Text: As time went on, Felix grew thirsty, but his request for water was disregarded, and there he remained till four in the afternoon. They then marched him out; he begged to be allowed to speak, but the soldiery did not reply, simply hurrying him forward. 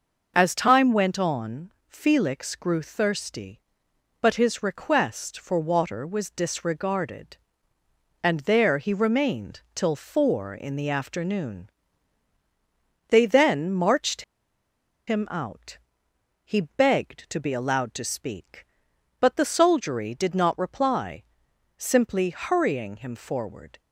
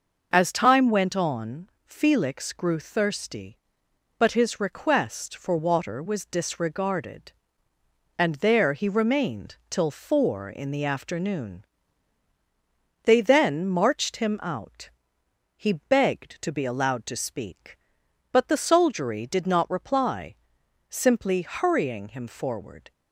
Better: second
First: pauses between "remained" and "till"; slight; at 9.5 s; 0.16 s long // pauses between "marched" and "him"; noticeable; at 14.2 s; 0.85 s long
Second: pauses between "remained" and "till"; slight; at 9.5 s; 0.16 s long

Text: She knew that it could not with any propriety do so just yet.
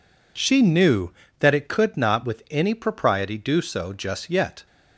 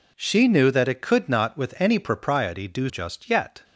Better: first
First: none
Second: skips "so"; at 2.8 s

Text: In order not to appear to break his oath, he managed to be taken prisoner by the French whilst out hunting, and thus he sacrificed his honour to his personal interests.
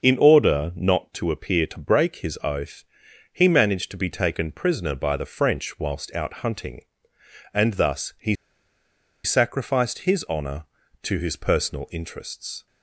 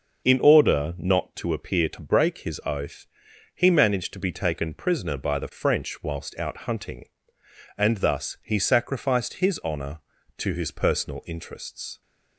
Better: second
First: starts louder than the rest; until 1.0 s; 6.5 dB // pauses between "he" and "sacrificed"; noticeable; at 8.3 s; 0.89 s long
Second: starts louder than the rest; until 1.3 s; 6.5 dB

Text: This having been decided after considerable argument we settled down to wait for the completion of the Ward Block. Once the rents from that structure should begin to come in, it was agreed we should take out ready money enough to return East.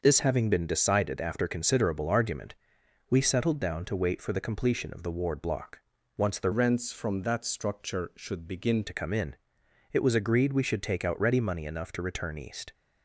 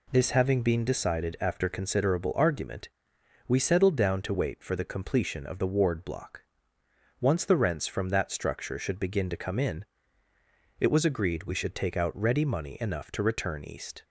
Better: second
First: starts louder than the rest; until 1.0 s; 6 dB // pauses between "argument" and "we"; noticeable; at 2.5 s; 0.54 s long // changes voice from "rents" to "begin"; from 6.5 to 8.8 s; 2.3 s long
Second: pauses between "argument" and "we"; noticeable; at 2.8 s; 0.58 s long

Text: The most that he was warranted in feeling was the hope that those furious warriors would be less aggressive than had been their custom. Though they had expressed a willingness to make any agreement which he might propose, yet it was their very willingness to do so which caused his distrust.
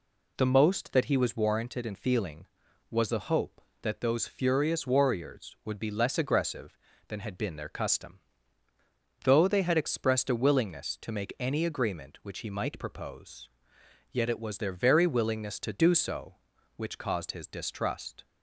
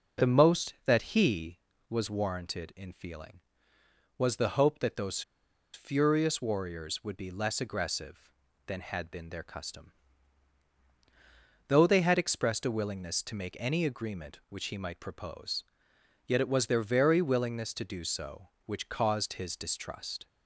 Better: first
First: none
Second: pauses between "those" and "furious"; noticeable; at 5.2 s; 0.52 s long

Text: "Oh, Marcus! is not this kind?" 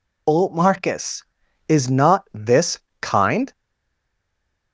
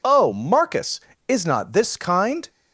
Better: second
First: pauses between "this" and "kind"; slight; at 2.7 s; 0.24 s long // stays silent after the last word; noticeable; from 3.5 s on; 1.2 s long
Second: none

